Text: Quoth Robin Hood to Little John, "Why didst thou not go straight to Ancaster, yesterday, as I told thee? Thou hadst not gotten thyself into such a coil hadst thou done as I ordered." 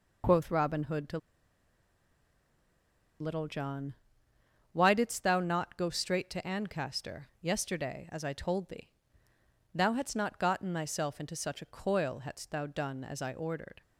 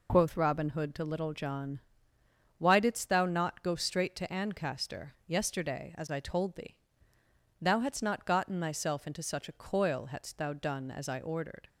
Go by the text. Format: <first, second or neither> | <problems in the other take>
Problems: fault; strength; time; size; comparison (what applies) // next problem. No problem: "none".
second | pauses between "to" and "Little"; strong; at 1.1 s; 2.0 s long